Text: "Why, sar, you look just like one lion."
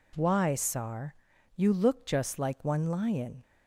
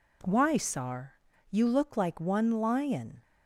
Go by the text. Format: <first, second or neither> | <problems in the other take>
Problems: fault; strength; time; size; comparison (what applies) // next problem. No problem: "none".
first | skips "just"; at 1.9 s